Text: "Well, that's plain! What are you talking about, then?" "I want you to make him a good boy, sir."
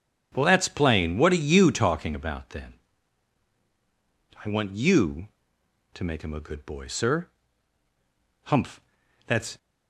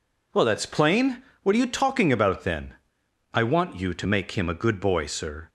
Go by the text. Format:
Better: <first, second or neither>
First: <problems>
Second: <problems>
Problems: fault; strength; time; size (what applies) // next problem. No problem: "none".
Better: second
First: starts louder than the rest; strong; until 1.3 s; 9 dB // goes on to say "Humph that's"; noticeable; from 8.4 s on; 1.1 s long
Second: none